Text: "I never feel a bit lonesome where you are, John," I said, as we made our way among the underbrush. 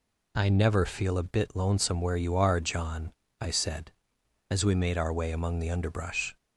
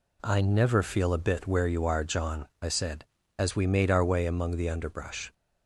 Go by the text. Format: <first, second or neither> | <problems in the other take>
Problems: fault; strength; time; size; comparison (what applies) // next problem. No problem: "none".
first | skips "lonesome"; at 1.4 s